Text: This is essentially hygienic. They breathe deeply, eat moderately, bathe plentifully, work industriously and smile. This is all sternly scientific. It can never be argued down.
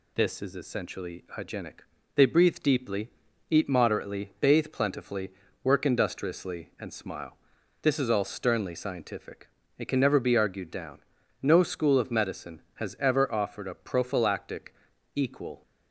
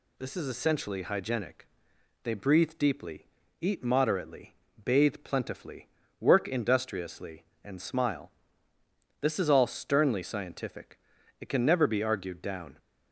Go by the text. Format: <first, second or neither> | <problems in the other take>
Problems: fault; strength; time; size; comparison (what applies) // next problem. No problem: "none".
second | goes on to say "No school of medicine has ever offered a prophylactic equal"; strong; from 11.4 s on; 4.2 s long